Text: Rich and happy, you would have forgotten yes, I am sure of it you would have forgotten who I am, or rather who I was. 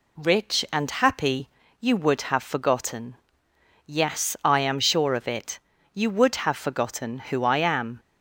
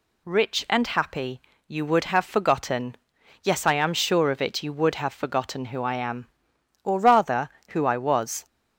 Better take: second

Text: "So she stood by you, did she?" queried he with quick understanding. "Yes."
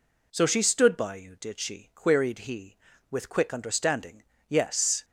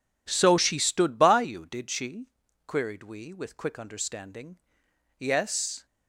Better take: first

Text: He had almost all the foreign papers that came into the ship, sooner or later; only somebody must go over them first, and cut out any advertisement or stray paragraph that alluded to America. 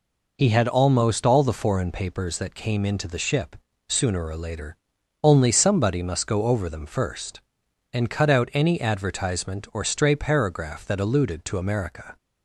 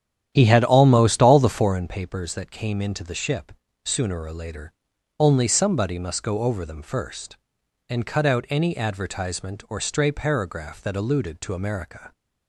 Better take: first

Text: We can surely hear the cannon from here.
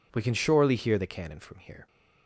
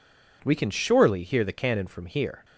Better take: neither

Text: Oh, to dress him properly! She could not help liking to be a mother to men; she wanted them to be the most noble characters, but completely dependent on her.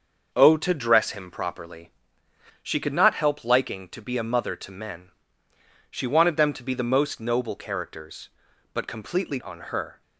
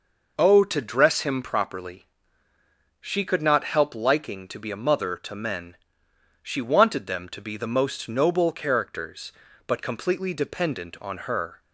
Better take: second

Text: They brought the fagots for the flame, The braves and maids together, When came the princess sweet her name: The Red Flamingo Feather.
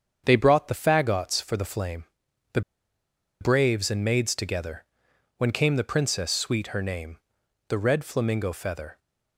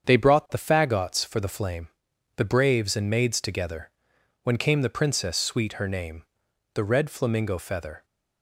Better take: second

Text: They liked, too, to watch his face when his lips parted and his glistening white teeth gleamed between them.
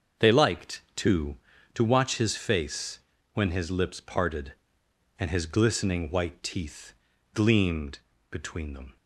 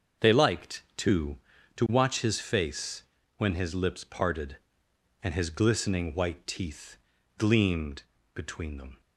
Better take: neither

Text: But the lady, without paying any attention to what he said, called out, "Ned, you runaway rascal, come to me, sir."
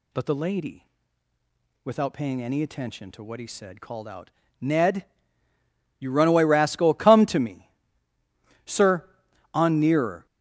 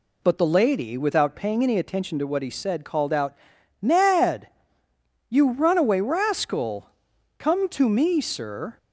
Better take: second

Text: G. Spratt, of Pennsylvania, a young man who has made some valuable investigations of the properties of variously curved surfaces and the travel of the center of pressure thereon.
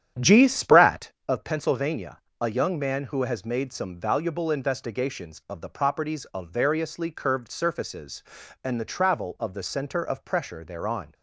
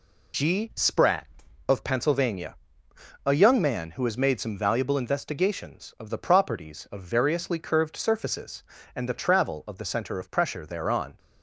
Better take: second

